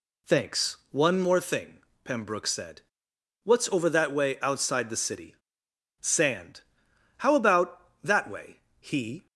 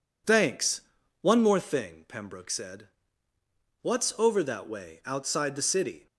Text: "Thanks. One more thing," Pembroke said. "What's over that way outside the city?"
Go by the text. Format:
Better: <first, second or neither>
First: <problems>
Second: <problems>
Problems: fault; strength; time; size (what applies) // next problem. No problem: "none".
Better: second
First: goes on to say "Sand How about that way he"; strong; from 6.0 s on; 3.2 s long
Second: none